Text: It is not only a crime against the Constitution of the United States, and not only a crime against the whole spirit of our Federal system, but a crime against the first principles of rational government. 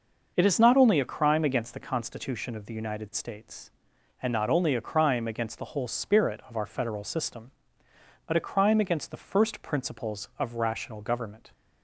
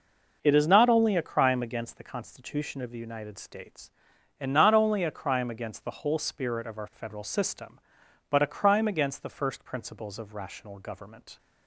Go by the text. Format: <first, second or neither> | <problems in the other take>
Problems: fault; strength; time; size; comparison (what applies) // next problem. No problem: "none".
neither | none